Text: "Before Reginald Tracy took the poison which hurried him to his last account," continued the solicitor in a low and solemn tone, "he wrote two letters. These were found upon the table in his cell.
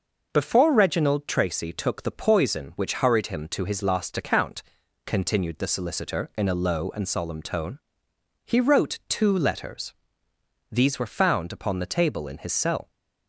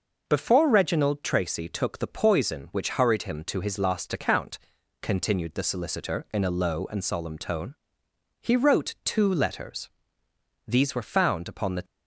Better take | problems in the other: first | stops before "table in his cell"; at 11.8 s

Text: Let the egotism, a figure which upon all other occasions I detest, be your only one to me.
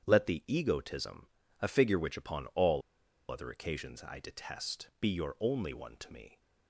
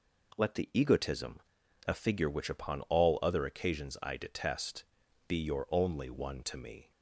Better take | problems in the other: second | starts louder than the rest; strong; until 1.0 s; 8.5 dB // pauses between "all" and "other"; noticeable; at 2.8 s; 0.50 s long

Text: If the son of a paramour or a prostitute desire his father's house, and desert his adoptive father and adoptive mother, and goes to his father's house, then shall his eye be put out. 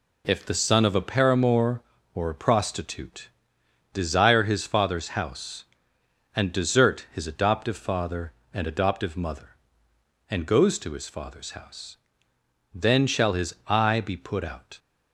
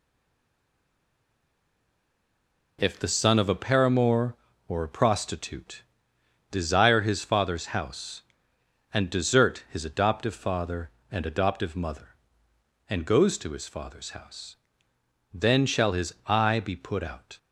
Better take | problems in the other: first | stays silent before the first word; strong; until 2.7 s; 2.7 s long // pauses between "prostitute" and "desire"; noticeable; at 5.8 s; 0.70 s long; noticeable in the first

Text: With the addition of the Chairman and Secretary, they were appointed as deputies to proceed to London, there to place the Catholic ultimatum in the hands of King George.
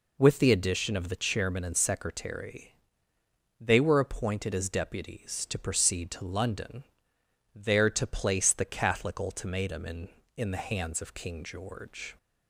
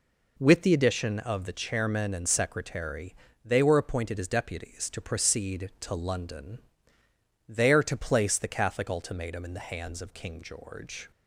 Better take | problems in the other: second | says "in" twice; at 10.3 s

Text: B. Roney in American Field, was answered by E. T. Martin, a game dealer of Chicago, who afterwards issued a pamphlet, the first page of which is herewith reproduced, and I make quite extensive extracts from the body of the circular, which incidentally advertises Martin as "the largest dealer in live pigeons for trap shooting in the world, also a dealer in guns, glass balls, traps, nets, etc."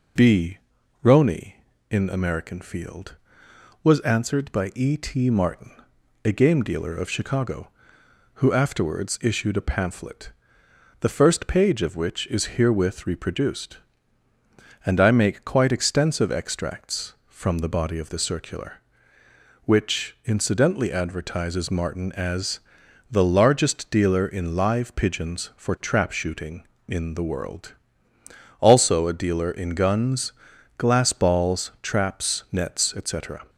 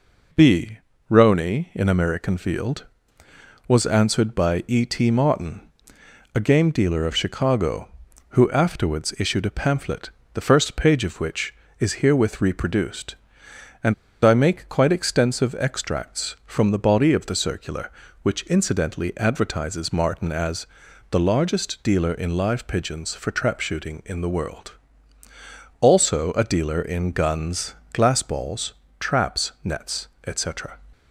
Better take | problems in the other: first | pauses between "and" and "I"; slight; at 13.9 s; 0.30 s long // pauses between "as" and "the"; noticeable; at 20.6 s; 0.46 s long; noticeable in the first

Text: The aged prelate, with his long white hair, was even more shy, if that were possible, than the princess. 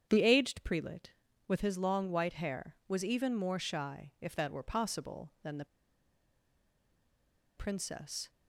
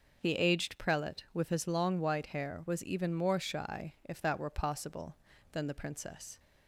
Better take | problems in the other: second | starts louder than the rest; strong; until 1.1 s; 8 dB; also in the second // pauses between "the" and "princess"; strong; at 5.6 s; 1.9 s long

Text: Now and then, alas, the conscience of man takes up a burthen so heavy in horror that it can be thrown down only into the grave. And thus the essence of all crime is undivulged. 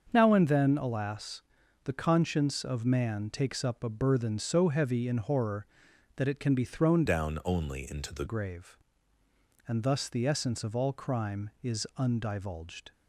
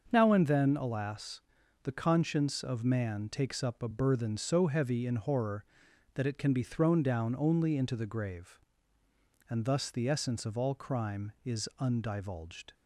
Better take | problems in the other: second | starts louder than the rest; until 1.1 s; 6.5 dB; also in the second // changes voice from "down" to "the"; from 7.0 to 8.2 s; 1.2 s long

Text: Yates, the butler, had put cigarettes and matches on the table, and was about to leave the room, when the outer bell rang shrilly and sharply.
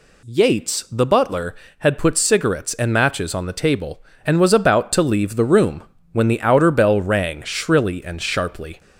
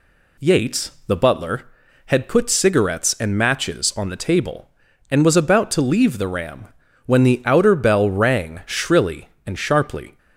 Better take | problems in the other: first | says "ram" for "room"; at 6.2 s

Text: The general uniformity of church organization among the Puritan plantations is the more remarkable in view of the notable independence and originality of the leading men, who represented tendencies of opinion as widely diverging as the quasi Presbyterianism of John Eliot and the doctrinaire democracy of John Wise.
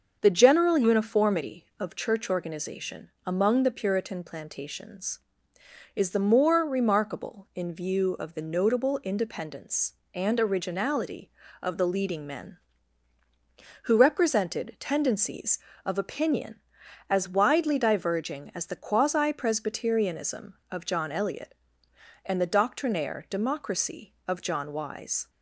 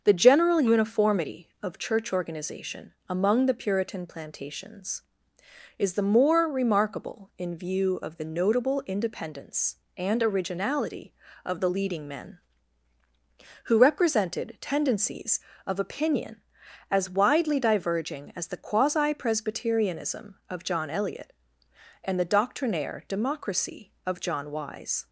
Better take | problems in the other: neither | starts louder than the rest; the same in both // pauses between "organization" and "among"; slight; the same in both

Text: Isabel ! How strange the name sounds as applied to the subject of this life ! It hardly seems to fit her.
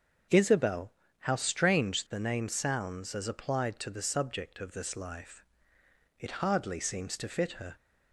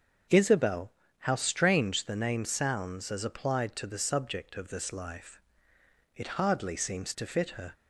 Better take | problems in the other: neither | starts louder than the rest; the same in both

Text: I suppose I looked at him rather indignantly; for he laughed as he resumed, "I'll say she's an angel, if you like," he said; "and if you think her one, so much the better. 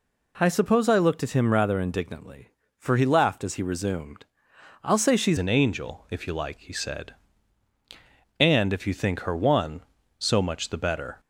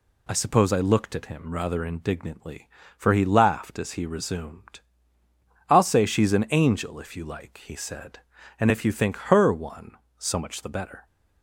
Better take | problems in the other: second | changes voice at "an"; from 5.3 s on; 5.8 s long

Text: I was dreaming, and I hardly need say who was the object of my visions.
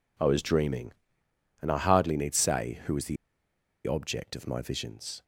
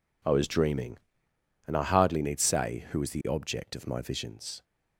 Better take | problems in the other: second | pauses between "the" and "object"; noticeable; at 3.1 s; 0.71 s long

